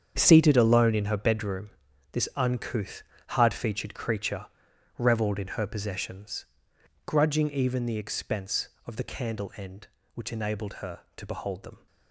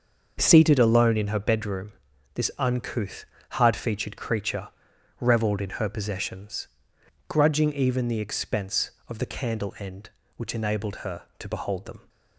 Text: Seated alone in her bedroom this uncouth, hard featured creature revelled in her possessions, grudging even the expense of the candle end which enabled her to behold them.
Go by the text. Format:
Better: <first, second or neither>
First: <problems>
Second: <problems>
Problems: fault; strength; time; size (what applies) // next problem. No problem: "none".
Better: second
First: gets quieter; strong; throughout; 13.5 dB // starts louder than the rest; strong; until 1.2 s; 7.5 dB // pauses between "bedroom" and "this"; at 1.6 s; 0.44 s long // pauses between "creature" and "revelled"; noticeable; at 4.4 s; 0.50 s long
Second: starts louder than the rest; until 1.4 s; 6 dB // pauses between "bedroom" and "this"; at 1.9 s; 0.44 s long // pauses between "creature" and "revelled"; noticeable; at 4.6 s; 0.50 s long